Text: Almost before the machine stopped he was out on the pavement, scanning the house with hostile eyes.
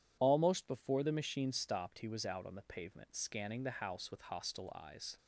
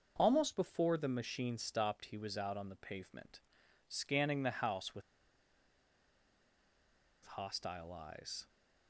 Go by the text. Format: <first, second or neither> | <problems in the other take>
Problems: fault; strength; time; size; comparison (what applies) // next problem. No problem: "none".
first | starts louder than the rest; noticeable; until 1.1 s; 6 dB // pauses between "with" and "hostile"; strong; at 5.0 s; 2.2 s long